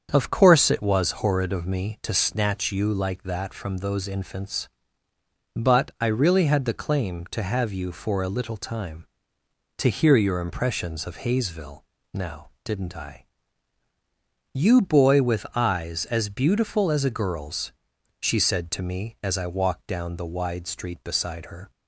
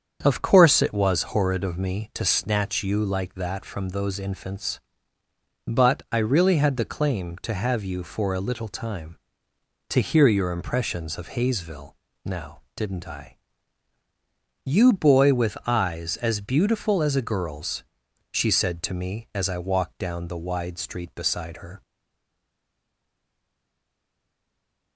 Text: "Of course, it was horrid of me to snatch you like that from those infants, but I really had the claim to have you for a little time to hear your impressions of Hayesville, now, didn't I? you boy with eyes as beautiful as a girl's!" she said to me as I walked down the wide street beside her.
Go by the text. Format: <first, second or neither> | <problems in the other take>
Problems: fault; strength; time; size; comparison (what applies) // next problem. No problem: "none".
first | starts louder than the rest; strong; until 1.2 s; 7.5 dB; strong in the first // stays silent after the last word; strong; from 21.8 s on; 3.1 s long